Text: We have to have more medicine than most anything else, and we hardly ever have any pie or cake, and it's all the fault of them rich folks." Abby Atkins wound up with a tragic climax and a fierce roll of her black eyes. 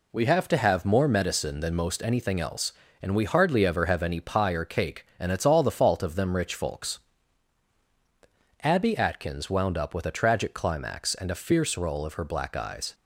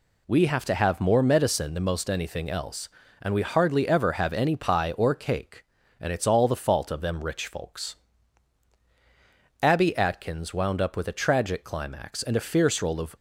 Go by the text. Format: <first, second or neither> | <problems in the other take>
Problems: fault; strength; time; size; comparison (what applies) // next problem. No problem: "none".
first | stops before "her black eyes"; at 13.1 s